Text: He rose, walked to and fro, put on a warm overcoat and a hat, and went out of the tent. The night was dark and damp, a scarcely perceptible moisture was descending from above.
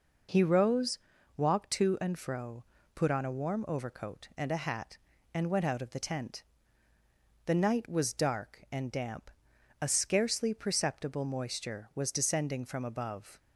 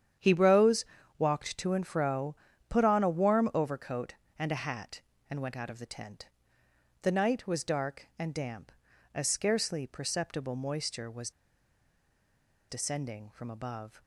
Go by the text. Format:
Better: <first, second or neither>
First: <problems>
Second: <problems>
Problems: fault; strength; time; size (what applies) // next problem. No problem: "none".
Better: first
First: none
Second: starts louder than the rest; strong; until 1.5 s; 9 dB // pauses between "was" and "descending"; strong; at 11.3 s; 1.3 s long